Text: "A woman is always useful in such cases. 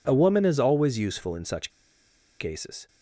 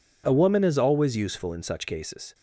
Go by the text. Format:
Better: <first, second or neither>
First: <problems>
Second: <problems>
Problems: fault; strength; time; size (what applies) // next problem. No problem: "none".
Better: second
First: pauses between "such" and "cases"; noticeable; at 1.6 s; 0.71 s long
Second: none